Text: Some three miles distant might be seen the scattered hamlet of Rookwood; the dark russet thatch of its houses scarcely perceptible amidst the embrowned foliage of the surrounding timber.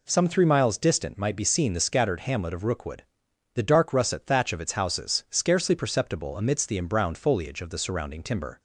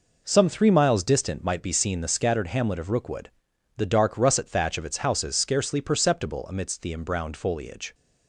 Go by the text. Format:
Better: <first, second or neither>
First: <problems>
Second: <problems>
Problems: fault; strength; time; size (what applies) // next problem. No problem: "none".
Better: first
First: none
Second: stops before "of the surrounding timber"; at 7.9 s